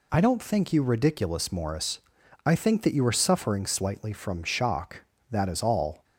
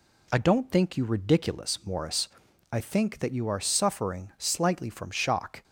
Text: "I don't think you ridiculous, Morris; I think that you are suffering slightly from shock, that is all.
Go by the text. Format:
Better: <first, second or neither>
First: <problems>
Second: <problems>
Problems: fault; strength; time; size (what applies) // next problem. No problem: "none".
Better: first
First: none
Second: stops before "that is all"; at 5.6 s